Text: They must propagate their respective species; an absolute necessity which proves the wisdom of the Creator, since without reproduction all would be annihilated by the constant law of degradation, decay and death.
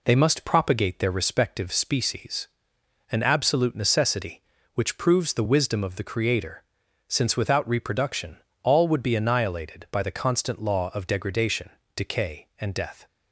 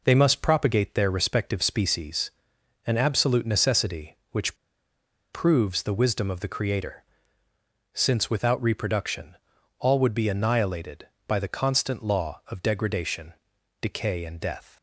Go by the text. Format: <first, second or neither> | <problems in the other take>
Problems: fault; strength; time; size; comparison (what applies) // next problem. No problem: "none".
first | pauses between "which" and "proves"; noticeable; at 4.5 s; 0.76 s long // pauses between "reproduction" and "all"; noticeable; at 9.3 s; 0.46 s long; slight in the first